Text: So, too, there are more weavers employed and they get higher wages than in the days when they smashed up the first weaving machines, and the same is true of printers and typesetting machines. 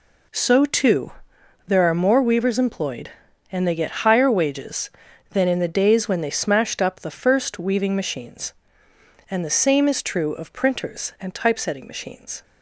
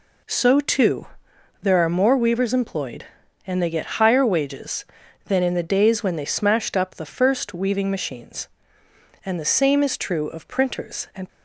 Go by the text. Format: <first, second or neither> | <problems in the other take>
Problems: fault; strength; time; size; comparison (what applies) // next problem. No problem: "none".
first | stops before "typesetting machines"; at 11.2 s